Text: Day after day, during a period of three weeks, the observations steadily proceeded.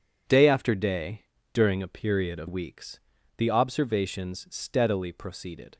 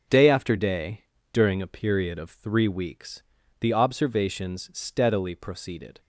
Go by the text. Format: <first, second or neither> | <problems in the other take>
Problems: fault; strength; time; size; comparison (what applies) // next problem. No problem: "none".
second | skips "three"; at 2.4 s